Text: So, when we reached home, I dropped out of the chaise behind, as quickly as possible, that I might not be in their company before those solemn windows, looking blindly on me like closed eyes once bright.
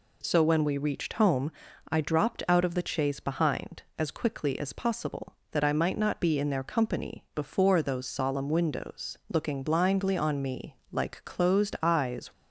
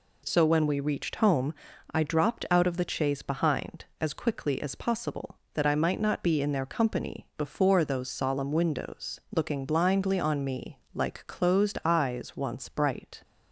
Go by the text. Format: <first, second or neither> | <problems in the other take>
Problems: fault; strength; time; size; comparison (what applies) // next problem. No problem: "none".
second | pauses between "me" and "like"; slight; at 10.7 s; 0.16 s long; slight in the second // stops before "once bright"; at 12.3 s